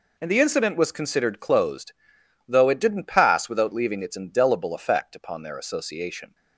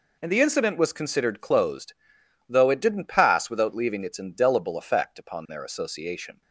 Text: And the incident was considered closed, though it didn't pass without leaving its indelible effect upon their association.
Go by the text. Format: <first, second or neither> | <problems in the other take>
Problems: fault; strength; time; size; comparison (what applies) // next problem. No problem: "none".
neither | none